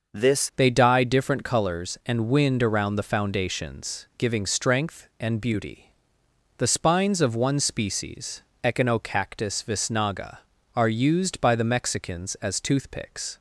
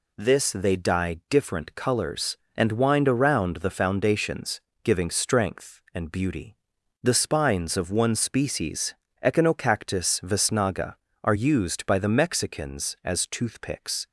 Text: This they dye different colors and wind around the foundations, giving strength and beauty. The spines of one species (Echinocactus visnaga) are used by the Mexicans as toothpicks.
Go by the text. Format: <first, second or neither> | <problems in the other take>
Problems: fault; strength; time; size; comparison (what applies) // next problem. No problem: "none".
second | starts louder than the rest; noticeable; until 1.2 s; 6 dB // changes voice at "they"; from 0.5 s on; 12.8 s long